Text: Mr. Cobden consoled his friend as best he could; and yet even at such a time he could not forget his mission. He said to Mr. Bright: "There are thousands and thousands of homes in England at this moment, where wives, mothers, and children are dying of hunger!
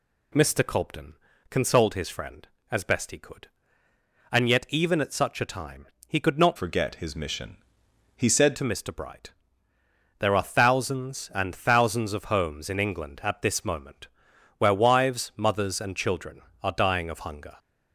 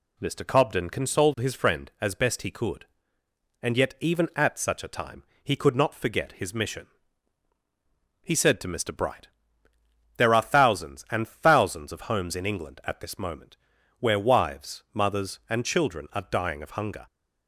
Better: second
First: pauses between "Cobden" and "consoled"; at 1.1 s; 0.38 s long // pauses between "time" and "he"; slight; at 5.8 s; 0.20 s long // changes voice from "forget" to "said"; from 6.5 to 8.5 s; 2.0 s long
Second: pauses between "time" and "he"; slight; at 5.2 s; 0.18 s long

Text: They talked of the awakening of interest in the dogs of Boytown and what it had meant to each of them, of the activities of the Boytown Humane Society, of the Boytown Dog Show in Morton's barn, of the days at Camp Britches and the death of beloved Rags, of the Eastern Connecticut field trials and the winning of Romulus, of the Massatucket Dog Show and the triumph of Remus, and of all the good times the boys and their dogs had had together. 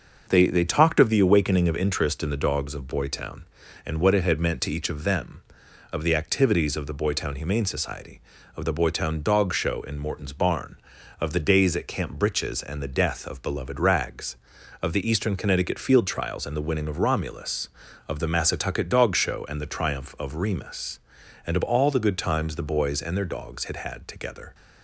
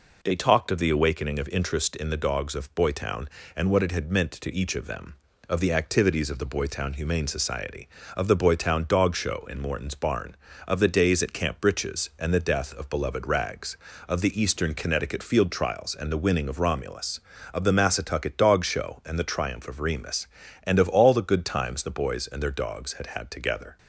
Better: second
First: starts louder than the rest; noticeable; until 1.2 s; 6 dB // says "They" twice; at 0.4 s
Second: none

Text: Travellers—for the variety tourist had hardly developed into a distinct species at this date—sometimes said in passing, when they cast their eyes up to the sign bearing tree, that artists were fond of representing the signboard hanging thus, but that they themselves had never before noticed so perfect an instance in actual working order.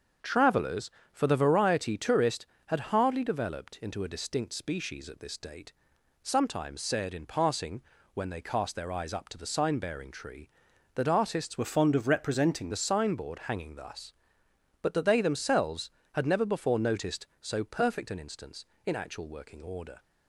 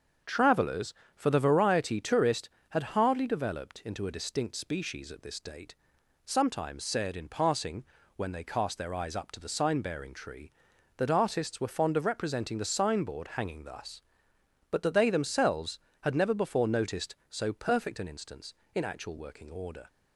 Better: second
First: starts louder than the rest; until 1.4 s; 7 dB // changes voice from "were" to "representing"; from 11.5 to 12.7 s; 1.2 s long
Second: starts louder than the rest; until 1.4 s; 7 dB

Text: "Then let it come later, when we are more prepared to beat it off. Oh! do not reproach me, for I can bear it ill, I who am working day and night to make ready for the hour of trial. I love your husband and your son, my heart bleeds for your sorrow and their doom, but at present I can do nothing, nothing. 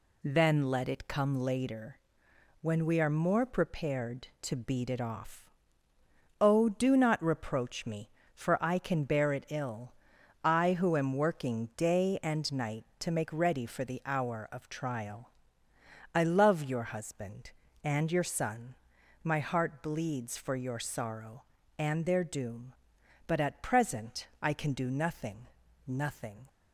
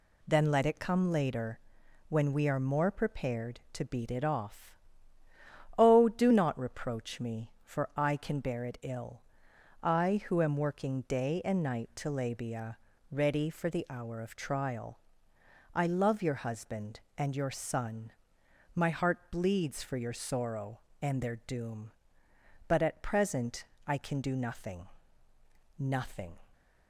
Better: first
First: pauses between "present" and "I"; slight; at 24.2 s; 0.16 s long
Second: says "labia" for "make"; at 12.0 s // pauses between "present" and "I"; slight; at 23.6 s; 0.22 s long

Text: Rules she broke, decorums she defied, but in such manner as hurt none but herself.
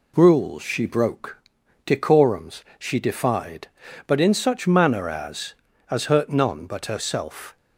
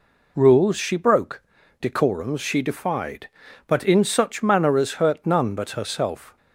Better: second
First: pauses between "decorums" and "she"; slight; at 2.6 s; 0.16 s long // says "as" twice; at 5.9 s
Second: none

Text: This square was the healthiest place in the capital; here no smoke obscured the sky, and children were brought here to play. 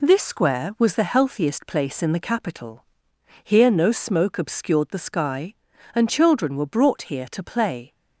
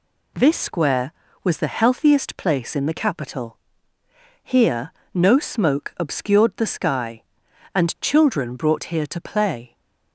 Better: first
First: none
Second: pauses between "here" and "no"; slight; at 4.9 s; 0.22 s long // skips "were"; at 8.5 s

